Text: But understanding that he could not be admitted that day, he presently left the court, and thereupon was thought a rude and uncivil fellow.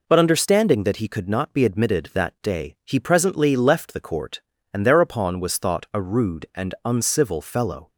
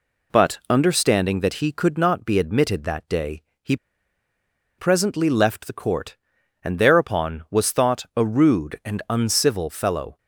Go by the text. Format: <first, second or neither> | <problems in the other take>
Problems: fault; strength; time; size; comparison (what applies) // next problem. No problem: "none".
first | pauses between "he" and "presently"; at 3.7 s; 1.0 s long